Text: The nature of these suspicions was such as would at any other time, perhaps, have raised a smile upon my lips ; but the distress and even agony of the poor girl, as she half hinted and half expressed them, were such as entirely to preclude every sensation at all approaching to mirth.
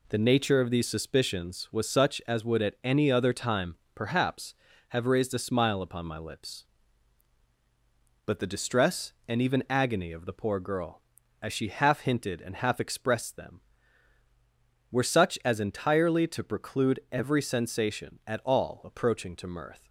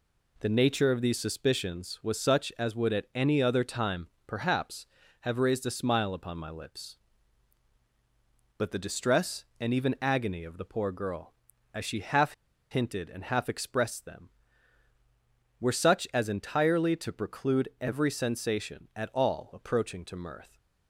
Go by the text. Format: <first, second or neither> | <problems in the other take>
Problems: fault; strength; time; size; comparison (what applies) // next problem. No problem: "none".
first | pauses between "half" and "hinted"; at 12.3 s; 0.38 s long